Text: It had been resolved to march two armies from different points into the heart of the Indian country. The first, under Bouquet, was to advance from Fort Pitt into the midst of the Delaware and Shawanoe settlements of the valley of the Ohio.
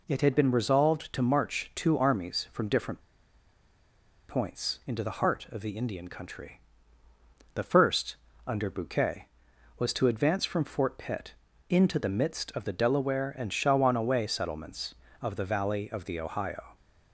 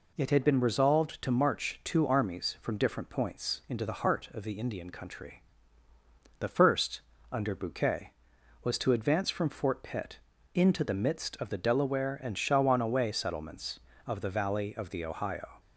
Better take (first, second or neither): second